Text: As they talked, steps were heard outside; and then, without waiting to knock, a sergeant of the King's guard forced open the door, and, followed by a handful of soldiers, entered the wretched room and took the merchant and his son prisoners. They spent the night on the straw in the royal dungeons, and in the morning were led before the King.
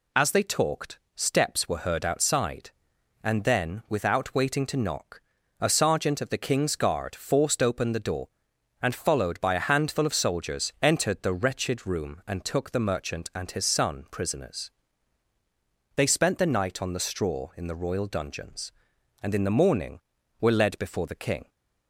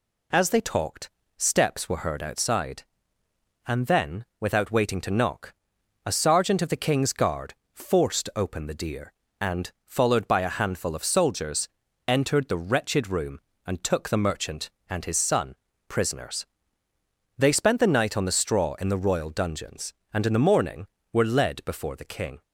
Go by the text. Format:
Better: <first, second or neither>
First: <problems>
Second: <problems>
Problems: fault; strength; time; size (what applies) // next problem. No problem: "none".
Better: first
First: none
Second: pauses between "guard" and "forced"; slight; at 7.5 s; 0.20 s long // says "deer" for "door"; at 8.7 s // pauses between "son" and "prisoners"; slight; at 15.5 s; 0.36 s long